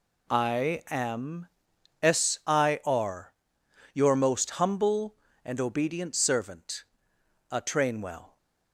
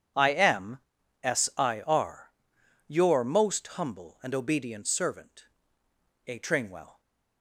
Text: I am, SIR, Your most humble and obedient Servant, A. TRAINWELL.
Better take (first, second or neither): neither